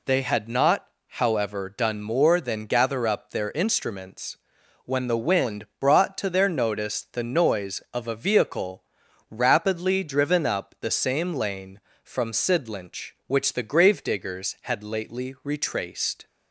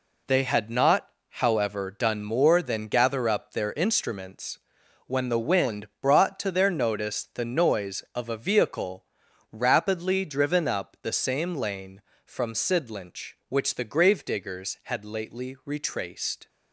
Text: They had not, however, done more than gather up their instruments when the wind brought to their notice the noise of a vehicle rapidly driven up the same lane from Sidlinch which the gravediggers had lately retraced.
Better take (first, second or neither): first